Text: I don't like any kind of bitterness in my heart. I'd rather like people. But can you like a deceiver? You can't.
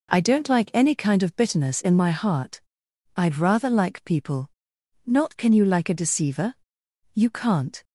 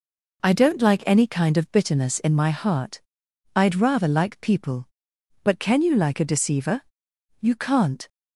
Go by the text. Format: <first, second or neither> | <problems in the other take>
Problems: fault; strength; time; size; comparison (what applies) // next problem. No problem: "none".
second | says "Not" for "But"; at 5.0 s